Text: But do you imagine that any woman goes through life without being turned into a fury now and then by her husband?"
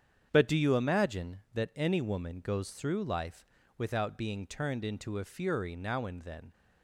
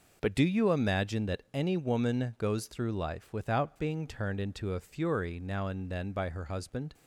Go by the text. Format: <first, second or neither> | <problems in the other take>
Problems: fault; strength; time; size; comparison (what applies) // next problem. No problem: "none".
second | starts louder than the rest; strong; until 1.3 s; 8.5 dB // pauses between "life" and "without"; slight; at 3.4 s; 0.32 s long // stops before "by her husband"; at 6.5 s